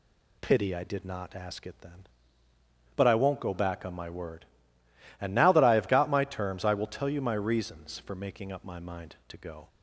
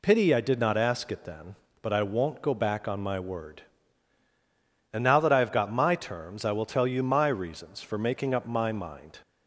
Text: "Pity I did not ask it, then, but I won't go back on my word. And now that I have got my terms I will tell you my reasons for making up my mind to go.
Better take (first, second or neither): first